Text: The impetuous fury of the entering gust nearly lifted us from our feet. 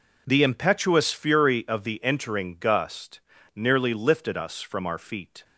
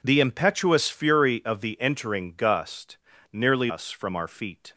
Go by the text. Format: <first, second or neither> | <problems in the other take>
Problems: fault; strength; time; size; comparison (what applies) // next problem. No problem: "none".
first | pauses between "gust" and "nearly"; slight; at 2.9 s; 0.34 s long; slight in the first // skips "lifted"; at 3.6 s